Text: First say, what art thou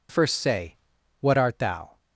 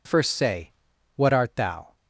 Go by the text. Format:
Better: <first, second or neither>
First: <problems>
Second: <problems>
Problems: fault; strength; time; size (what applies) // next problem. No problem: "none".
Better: neither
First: none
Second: none